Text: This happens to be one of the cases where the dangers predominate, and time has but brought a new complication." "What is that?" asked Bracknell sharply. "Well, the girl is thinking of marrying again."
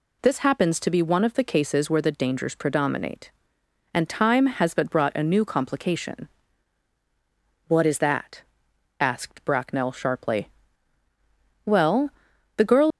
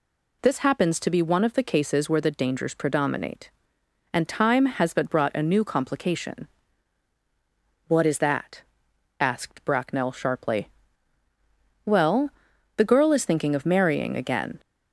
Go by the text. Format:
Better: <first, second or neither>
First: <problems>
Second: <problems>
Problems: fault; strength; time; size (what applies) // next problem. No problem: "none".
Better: second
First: stops before "is thinking of marrying again"; at 12.9 s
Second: none